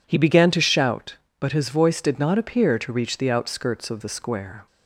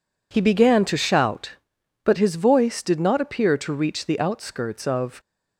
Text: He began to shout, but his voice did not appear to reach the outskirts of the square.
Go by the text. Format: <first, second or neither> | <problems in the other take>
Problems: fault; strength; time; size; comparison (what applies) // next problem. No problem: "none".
first | stops before "the square"; at 5.1 s